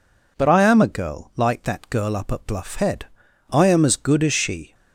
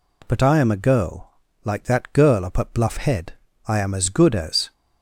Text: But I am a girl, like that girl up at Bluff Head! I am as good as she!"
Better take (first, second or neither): first